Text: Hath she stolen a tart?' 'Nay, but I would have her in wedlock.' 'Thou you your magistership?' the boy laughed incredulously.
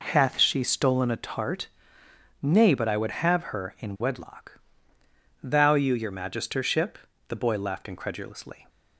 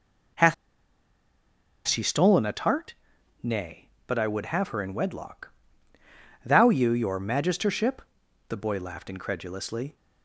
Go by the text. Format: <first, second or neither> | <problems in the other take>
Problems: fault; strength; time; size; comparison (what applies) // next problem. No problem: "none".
first | pauses between "Hath" and "she"; strong; at 0.5 s; 1.3 s long